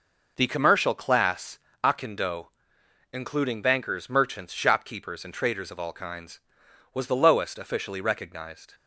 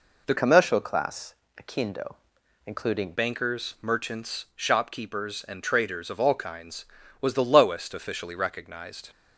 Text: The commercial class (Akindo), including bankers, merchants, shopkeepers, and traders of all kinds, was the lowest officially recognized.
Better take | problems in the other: first | changes voice from "commercial" to "including"; from 0.3 to 3.1 s; 2.8 s long

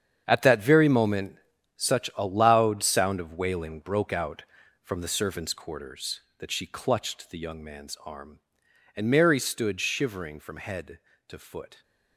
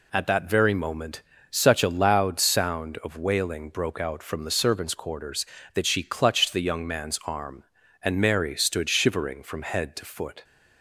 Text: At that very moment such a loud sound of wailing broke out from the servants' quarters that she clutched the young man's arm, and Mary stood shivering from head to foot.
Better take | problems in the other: second | gets quieter; strong; throughout; 13 dB // pauses between "moment" and "such"; at 1.3 s; 0.38 s long; slight in the second

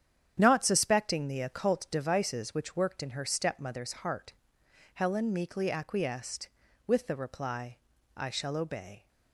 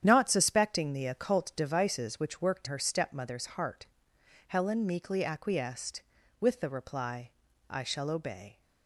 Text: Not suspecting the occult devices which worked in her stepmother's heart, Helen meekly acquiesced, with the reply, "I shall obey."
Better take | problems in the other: first | starts louder than the rest; strong; until 1.0 s; 9.5 dB; strong in the first // skips "in"; at 2.6 s

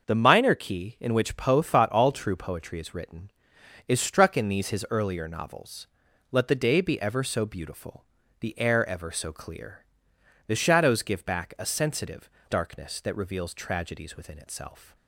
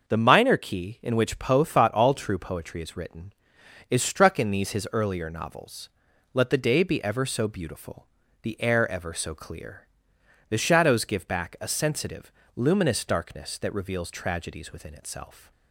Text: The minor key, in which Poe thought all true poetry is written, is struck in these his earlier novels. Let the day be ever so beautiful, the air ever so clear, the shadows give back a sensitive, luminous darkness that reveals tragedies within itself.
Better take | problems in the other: second | starts louder than the rest; noticeable; until 1.0 s; 6 dB; noticeable in the second // skips "luminous"; at 12.3 s

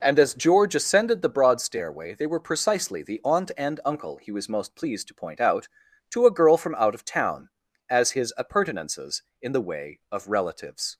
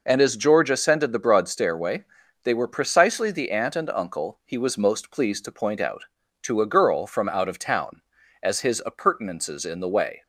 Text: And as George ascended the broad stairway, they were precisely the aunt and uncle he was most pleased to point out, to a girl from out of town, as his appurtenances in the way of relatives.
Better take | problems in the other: first | stops before "of relatives"; at 10.2 s

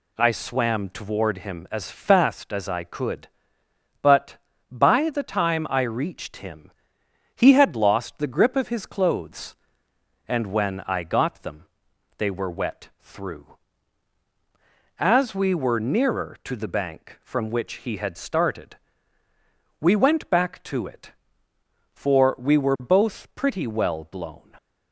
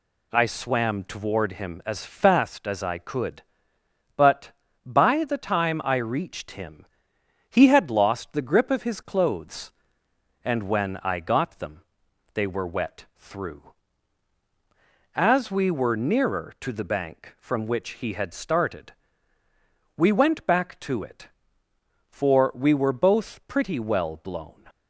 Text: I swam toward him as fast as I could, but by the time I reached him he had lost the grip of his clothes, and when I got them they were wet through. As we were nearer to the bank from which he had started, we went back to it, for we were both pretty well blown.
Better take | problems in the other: neither | pauses between "him" and "he"; noticeable; the same in both // pauses between "them" and "they"; noticeable; the same in both

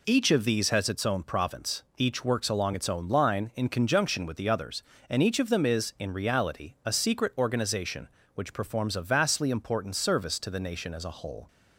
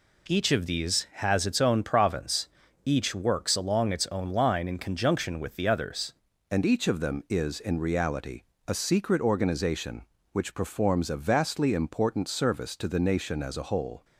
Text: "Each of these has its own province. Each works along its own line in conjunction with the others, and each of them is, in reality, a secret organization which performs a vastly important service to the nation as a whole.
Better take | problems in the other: first | changes voice at "and"; from 6.5 s on; 7.5 s long

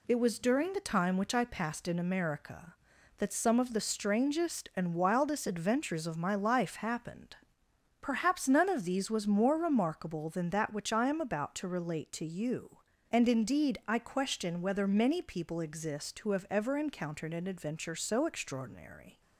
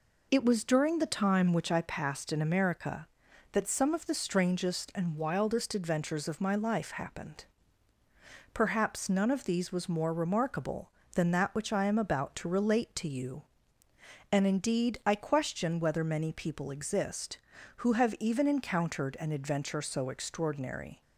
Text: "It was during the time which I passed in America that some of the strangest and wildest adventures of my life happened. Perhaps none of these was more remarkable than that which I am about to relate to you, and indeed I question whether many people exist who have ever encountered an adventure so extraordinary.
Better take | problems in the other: first | says "even" for "ever"; at 18.1 s

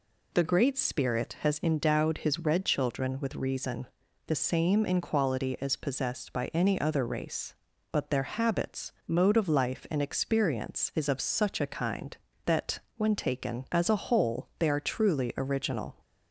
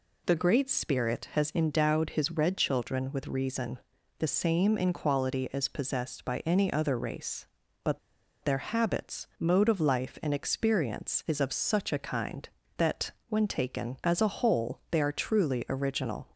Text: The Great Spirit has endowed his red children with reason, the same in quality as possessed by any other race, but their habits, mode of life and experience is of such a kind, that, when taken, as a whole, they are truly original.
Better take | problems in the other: first | pauses between "but" and "their"; at 7.9 s; 0.45 s long

